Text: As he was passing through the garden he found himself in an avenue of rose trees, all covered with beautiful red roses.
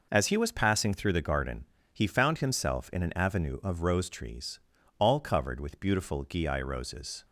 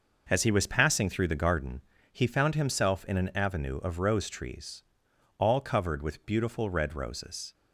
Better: second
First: pauses between "garden" and "he"; slight; at 1.6 s; 0.26 s long // says "gii" for "red"; at 6.2 s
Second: pauses between "garden" and "he"; slight; at 1.8 s; 0.30 s long

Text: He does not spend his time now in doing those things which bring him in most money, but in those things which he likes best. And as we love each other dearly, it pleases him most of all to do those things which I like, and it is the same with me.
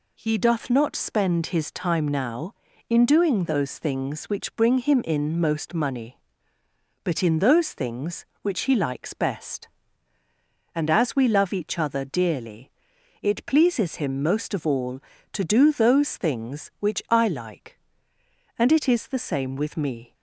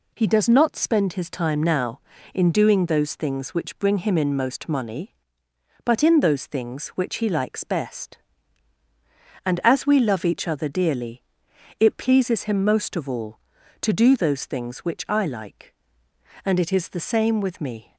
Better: second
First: says "doth" for "does"; at 0.3 s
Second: none

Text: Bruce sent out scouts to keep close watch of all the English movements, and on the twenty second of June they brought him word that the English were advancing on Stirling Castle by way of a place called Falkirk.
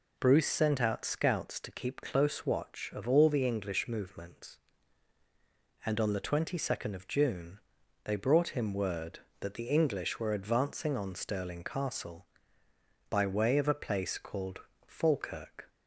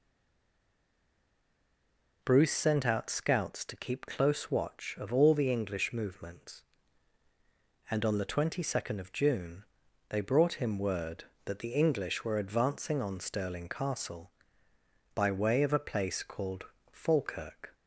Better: first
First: pauses between "June" and "they"; noticeable; at 7.5 s; 0.46 s long // pauses between "called" and "Falkirk"; slight; at 14.6 s; 0.26 s long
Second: stays silent before the first word; until 2.2 s; 2.2 s long // pauses between "June" and "they"; noticeable; at 9.6 s; 0.46 s long // pauses between "called" and "Falkirk"; slight; at 16.6 s; 0.26 s long

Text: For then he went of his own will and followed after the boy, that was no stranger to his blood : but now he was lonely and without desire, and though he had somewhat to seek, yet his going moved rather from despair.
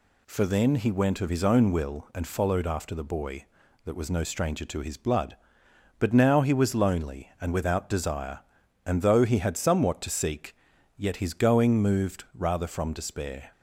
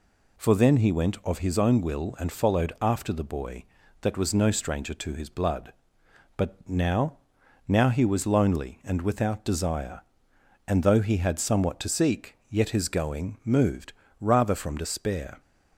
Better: first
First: none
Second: says "now" twice; at 7.6 s // pauses between "moved" and "rather"; slight; at 13.9 s; 0.26 s long

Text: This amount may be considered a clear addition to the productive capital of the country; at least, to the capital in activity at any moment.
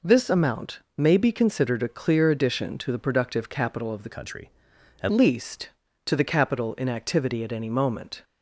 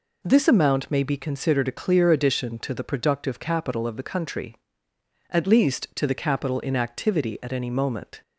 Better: second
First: pauses between "amount" and "may"; slight; at 0.7 s; 0.18 s long // changes voice from "country" to "at"; from 4.1 to 5.0 s; 0.9 s long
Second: none

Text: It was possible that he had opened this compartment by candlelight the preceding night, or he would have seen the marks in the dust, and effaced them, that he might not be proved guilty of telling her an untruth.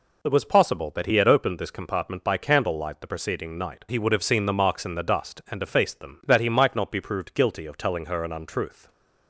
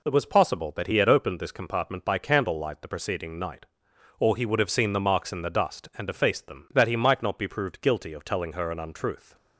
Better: second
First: skips "or"; at 3.8 s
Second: none

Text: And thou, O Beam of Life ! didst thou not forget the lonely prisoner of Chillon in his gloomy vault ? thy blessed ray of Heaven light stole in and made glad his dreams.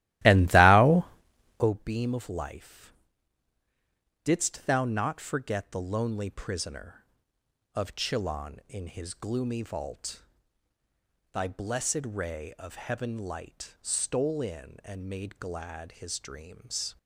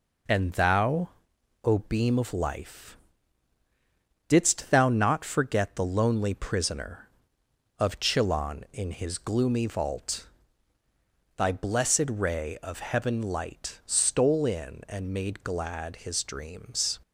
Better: second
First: starts louder than the rest; strong; until 1.7 s; 16 dB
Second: none

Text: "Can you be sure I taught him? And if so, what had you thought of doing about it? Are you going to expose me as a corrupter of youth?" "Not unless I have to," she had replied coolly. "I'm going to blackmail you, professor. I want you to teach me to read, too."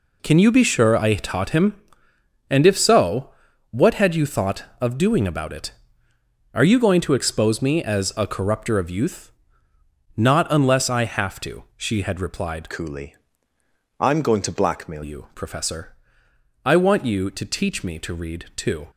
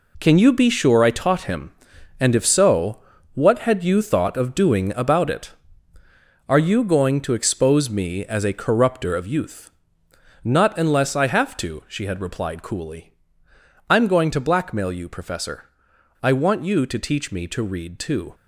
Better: second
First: changes voice from "coolly" to "blackmail"; from 12.6 to 15.0 s; 2.4 s long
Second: none

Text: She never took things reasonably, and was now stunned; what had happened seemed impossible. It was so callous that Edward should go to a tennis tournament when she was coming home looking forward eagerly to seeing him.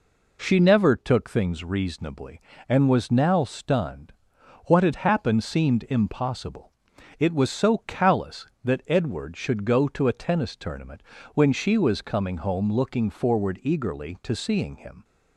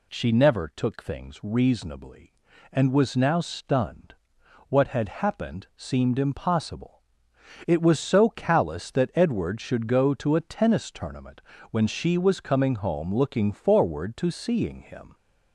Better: first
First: pauses between "tournament" and "when"; slight; at 11.0 s; 0.32 s long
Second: pauses between "tournament" and "when"; slight; at 11.4 s; 0.30 s long // skips "eagerly"; at 14.1 s

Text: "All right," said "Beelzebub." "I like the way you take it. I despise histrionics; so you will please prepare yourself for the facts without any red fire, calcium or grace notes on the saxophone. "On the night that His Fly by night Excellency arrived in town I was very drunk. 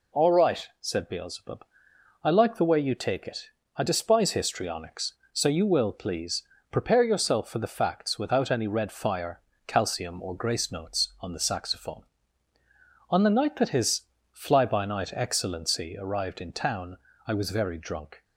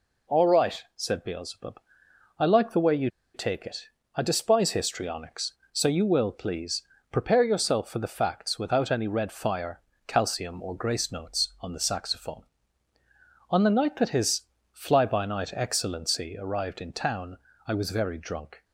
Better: first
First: pauses between "please" and "prepare"; slight; at 6.4 s; 0.29 s long // pauses between "His" and "Fly"; slight; at 14.0 s; 0.32 s long // pauses between "town" and "I"; slight; at 16.9 s; 0.28 s long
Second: pauses between "you" and "take"; slight; at 3.0 s; 0.25 s long // pauses between "please" and "prepare"; slight; at 6.8 s; 0.30 s long // pauses between "His" and "Fly"; slight; at 14.4 s; 0.32 s long // pauses between "town" and "I"; slight; at 17.3 s; 0.28 s long

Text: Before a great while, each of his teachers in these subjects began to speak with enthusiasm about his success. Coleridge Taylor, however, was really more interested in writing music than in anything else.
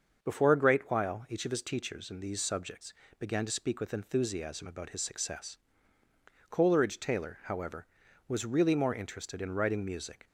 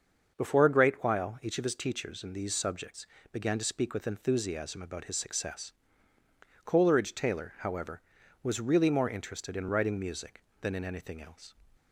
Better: second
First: starts louder than the rest; until 1.2 s; 6.5 dB // pauses between "subjects" and "began"; slight; at 2.9 s; 0.26 s long // stops before "than in anything else"; at 10.2 s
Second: starts louder than the rest; until 1.3 s; 6.5 dB // pauses between "subjects" and "began"; slight; at 3.0 s; 0.26 s long

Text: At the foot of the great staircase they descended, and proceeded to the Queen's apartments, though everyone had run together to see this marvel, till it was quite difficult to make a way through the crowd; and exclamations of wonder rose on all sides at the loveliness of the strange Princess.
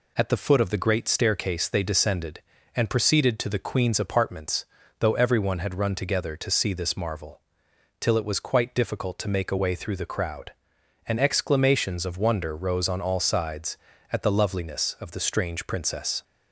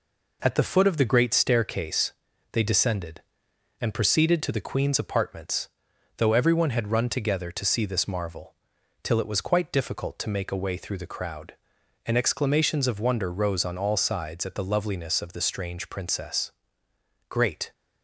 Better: first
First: none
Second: pauses between "staircase" and "they"; at 2.1 s; 0.40 s long // goes on to say "Great"; slight; from 17.2 s on; 0.44 s long

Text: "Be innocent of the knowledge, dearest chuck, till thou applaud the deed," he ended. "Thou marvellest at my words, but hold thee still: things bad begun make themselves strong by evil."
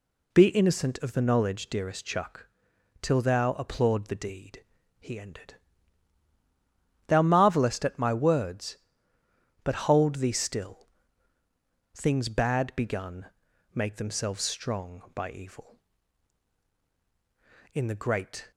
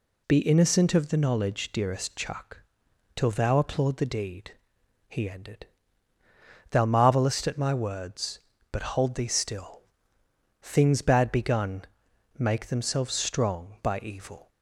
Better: second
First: pauses between "begun" and "make"; noticeable; at 13.2 s; 0.48 s long // goes on to say "In the great"; noticeable; from 17.7 s on; 0.78 s long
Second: pauses between "begun" and "make"; noticeable; at 11.8 s; 0.54 s long

